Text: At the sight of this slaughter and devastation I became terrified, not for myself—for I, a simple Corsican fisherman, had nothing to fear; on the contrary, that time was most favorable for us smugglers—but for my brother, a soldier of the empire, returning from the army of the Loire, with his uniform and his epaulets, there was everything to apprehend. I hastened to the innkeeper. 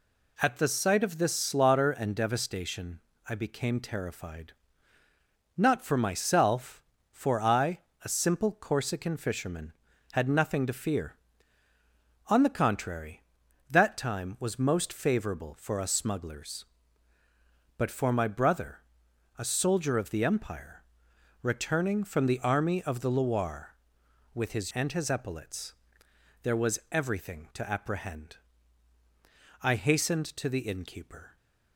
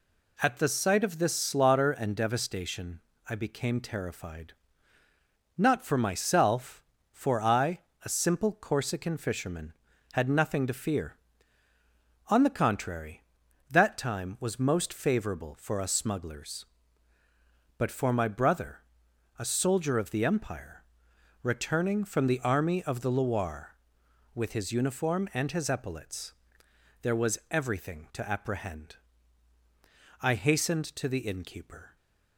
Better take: second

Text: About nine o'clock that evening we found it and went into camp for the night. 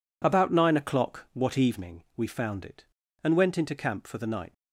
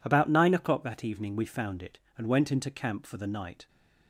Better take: second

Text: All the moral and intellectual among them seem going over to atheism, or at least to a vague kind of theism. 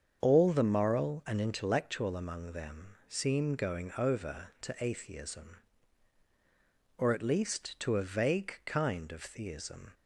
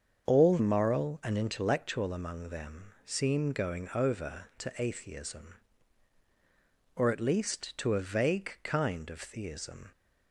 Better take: first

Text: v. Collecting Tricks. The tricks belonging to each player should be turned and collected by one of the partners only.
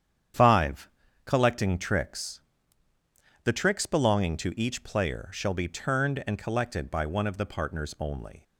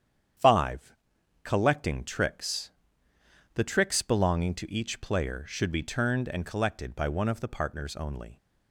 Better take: second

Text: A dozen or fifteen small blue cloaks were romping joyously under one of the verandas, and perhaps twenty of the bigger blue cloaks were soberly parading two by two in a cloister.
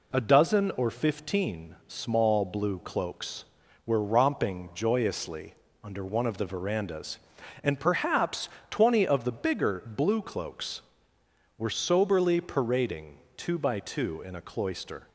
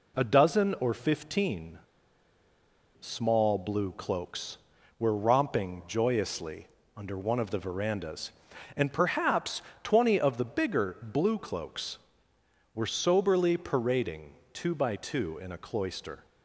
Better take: first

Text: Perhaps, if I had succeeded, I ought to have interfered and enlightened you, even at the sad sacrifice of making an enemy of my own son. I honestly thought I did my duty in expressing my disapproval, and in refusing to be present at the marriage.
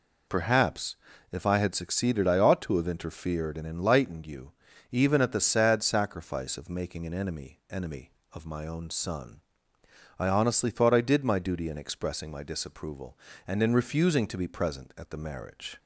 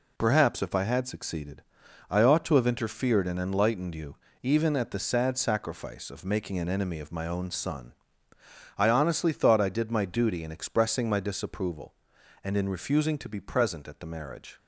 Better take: second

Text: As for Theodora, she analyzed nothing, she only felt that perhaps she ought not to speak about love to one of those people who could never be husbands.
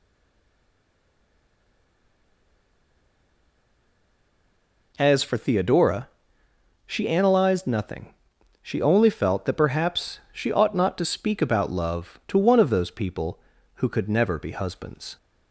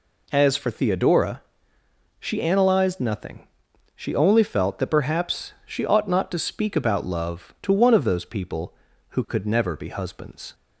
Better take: second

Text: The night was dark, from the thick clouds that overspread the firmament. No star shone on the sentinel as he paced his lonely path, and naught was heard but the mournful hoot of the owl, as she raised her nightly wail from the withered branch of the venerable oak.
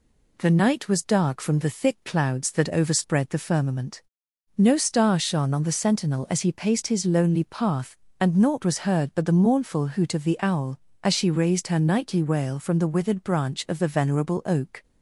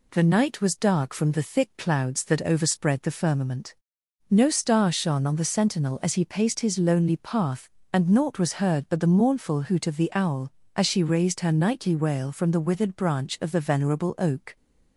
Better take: neither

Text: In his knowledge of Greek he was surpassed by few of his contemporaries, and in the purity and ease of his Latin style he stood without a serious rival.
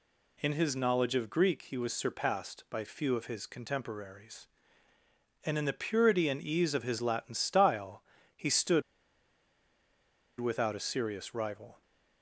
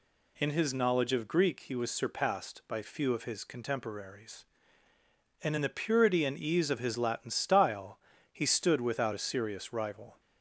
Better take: second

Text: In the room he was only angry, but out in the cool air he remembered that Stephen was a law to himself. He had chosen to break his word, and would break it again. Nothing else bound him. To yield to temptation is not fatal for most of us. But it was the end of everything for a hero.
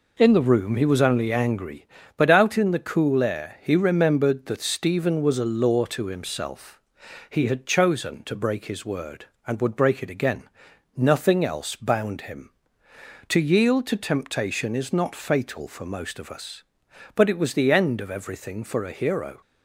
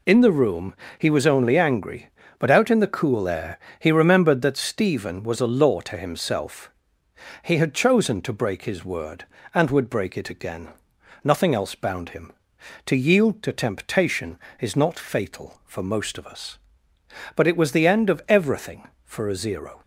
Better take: first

